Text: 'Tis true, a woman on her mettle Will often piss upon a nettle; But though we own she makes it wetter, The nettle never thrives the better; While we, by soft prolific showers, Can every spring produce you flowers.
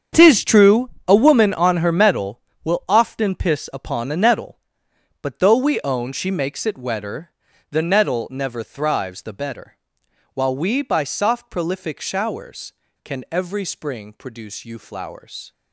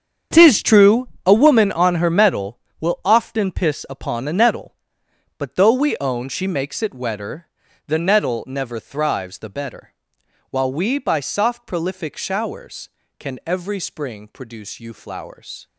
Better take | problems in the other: neither | starts louder than the rest; strong; the same in both

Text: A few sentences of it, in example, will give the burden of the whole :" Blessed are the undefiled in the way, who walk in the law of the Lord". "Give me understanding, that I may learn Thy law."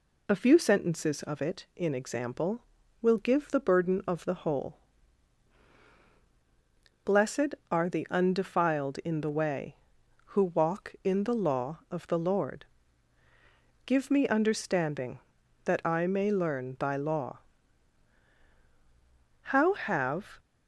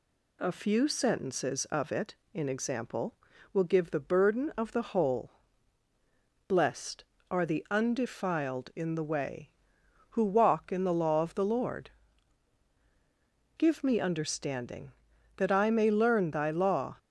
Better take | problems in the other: second | goes on to say "How have"; noticeable; from 19.4 s on; 0.98 s long

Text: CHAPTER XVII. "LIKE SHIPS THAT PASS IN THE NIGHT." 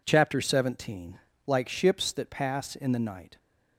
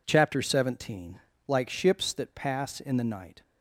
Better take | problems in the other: neither | none

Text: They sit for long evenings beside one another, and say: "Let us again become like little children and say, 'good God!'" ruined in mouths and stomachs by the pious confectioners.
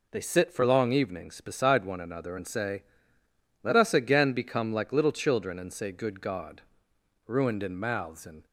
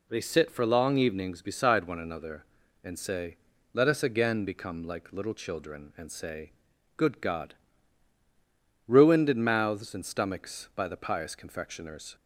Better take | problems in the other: second | stops before "stomachs by the pious confectioners"; at 8.4 s

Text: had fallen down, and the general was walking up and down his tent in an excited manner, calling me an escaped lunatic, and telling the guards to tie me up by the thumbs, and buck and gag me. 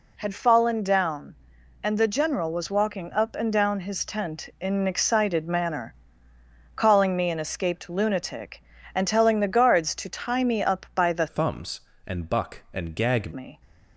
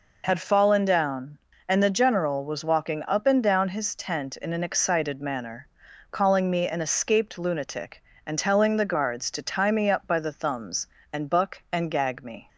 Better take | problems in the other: second | changes voice from "thumbs" to "gag"; from 11.2 to 13.3 s; 2.1 s long

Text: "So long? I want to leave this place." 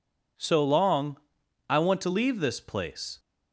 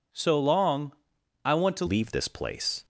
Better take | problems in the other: first | changes voice at "leave"; from 1.8 s on; 1.0 s long

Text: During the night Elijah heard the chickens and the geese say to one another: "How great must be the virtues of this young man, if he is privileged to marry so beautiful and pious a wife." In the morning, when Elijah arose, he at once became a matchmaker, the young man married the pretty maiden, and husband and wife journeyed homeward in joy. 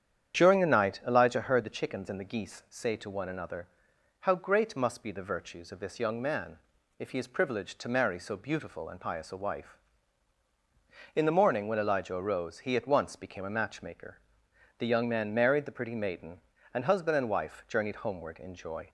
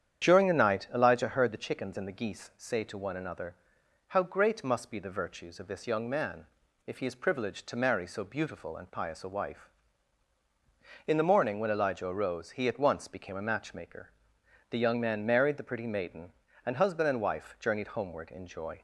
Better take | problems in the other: neither | starts louder than the rest; strong; the same in both

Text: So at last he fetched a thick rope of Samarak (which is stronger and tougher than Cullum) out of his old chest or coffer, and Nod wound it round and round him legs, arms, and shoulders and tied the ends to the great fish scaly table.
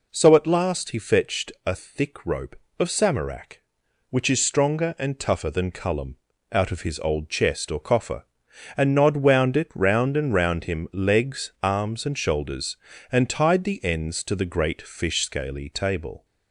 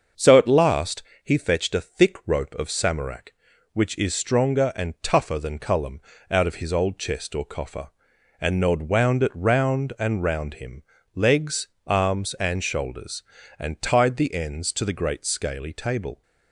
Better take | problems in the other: first | starts louder than the rest; until 1.3 s; 6.5 dB // pauses between "last" and "he"; slight; at 1.0 s; 0.22 s long // pauses between "him" and "legs"; slight; at 10.8 s; 0.30 s long // skips "fish"; at 15.2 s

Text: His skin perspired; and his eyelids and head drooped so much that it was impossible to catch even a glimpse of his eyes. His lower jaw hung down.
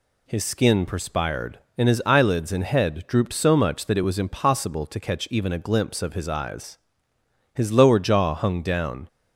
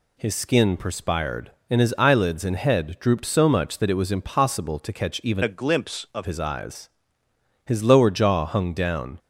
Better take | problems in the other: first | changes voice from "a" to "of"; from 5.4 to 6.2 s; 0.8 s long

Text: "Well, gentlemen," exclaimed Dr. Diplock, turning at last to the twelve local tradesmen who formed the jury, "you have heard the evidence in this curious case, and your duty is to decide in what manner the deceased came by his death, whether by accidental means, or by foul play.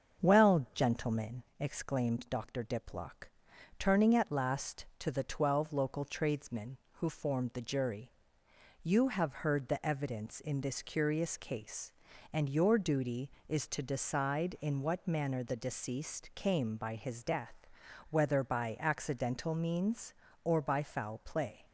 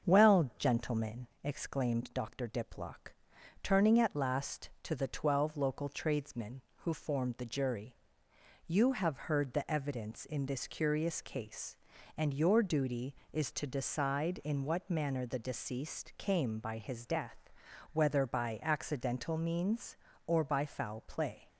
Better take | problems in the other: neither | starts louder than the rest; the same in both

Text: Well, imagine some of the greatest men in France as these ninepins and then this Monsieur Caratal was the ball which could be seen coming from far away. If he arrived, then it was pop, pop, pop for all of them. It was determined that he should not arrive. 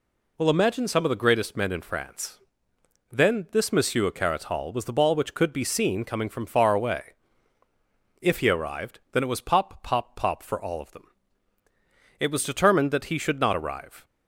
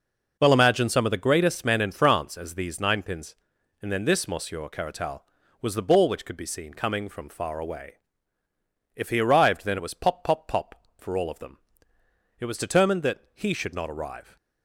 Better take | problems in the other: second | skips "as these ninepins and"; at 2.7 s

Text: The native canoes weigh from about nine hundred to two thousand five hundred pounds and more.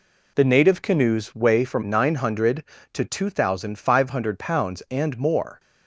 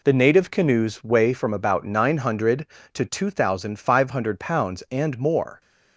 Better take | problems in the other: second | skips "about"; at 1.8 s

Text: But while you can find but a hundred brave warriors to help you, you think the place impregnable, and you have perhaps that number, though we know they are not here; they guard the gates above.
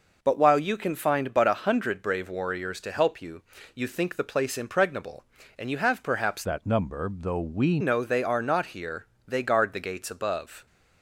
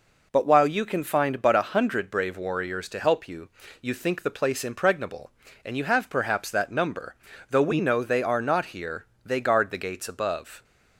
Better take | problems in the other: second | changes voice from "that" to "we"; from 6.4 to 7.7 s; 1.3 s long

